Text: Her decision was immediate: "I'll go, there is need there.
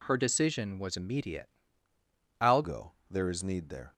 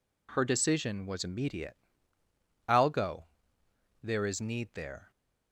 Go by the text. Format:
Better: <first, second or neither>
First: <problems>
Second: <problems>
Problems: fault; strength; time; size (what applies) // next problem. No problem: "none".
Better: second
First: changes voice at "go"; from 2.6 s on; 1.3 s long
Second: none